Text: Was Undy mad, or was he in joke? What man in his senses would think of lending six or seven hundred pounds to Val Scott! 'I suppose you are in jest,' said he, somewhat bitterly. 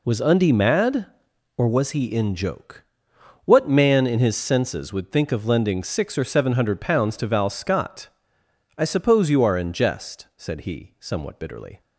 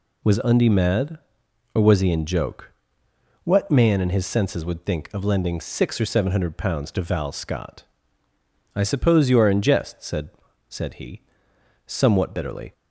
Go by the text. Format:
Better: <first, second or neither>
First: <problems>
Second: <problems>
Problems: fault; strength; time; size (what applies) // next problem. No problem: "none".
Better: first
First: none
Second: says "said" twice; at 10.6 s